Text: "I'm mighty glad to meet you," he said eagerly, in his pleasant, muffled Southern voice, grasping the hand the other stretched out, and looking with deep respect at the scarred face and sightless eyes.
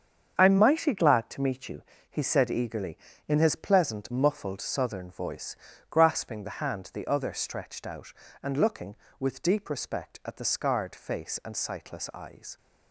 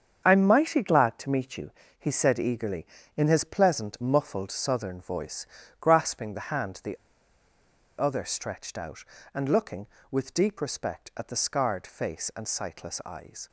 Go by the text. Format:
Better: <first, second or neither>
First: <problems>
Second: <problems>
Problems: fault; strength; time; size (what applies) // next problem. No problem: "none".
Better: first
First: starts louder than the rest; strong; until 1.3 s; 7.5 dB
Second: starts louder than the rest; strong; until 1.2 s; 7.5 dB // pauses between "the" and "other"; at 6.9 s; 1.0 s long